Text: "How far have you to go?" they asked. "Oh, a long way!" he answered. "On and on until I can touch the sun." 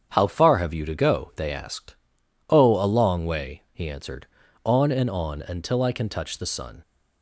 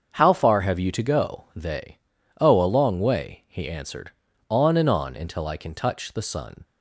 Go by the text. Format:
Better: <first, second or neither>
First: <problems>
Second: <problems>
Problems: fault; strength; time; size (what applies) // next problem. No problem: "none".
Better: first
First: starts louder than the rest; strong; until 1.1 s; 8 dB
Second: starts louder than the rest; until 1.1 s; 7 dB // skips "asked"; at 2.1 s